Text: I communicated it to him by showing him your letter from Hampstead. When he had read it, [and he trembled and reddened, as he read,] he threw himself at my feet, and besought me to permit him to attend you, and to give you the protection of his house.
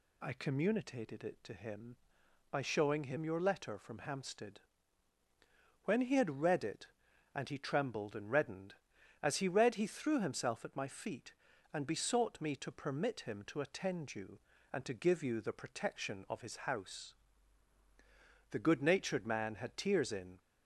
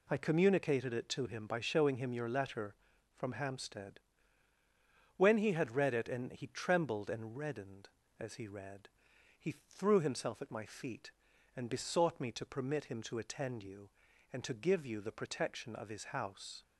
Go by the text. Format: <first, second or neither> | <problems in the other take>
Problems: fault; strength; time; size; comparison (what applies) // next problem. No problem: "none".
second | goes on to say "The good natured man had tears in"; strong; from 18.5 s on; 1.8 s long